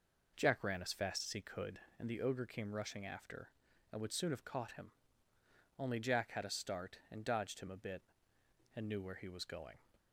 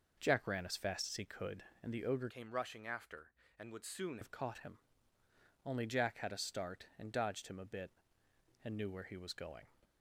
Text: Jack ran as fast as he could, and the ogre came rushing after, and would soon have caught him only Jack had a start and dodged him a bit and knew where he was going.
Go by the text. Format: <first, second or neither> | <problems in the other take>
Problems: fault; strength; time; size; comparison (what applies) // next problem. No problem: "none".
first | changes voice from "came" to "soon"; from 2.3 to 4.1 s; 1.8 s long // pauses between "him" and "only"; noticeable; at 4.7 s; 0.88 s long; noticeable in the first